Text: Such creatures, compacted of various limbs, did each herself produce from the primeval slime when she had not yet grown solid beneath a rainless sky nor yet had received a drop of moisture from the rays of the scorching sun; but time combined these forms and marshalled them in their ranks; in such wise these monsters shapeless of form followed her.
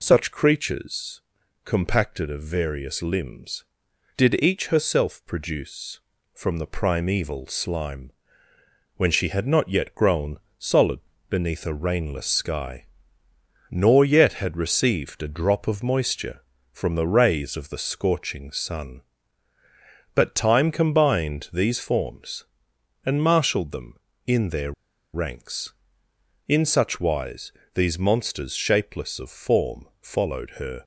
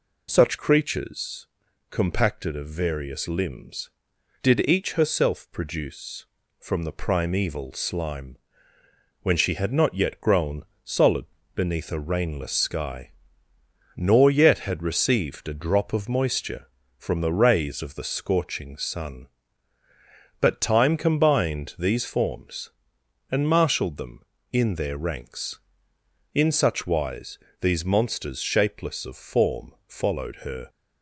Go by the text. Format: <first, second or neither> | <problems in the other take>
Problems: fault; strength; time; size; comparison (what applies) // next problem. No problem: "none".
second | pauses between "slime" and "when"; noticeable; at 8.0 s; 0.86 s long; noticeable in the second // pauses between "grown" and "solid"; slight; at 10.3 s; 0.20 s long; slight in the second // pauses between "solid" and "beneath"; slight; at 10.9 s; 0.32 s long; slight in the second // pauses between "sky" and "nor"; noticeable; at 12.8 s; 0.84 s long; noticeable in the second // pauses between "their" and "ranks"; at 24.7 s; 0.41 s long // pauses between "wise" and "these"; slight; at 27.5 s; 0.24 s long; slight in the second // pauses between "form" and "followed"; slight; at 29.8 s; 0.16 s long; slight in the second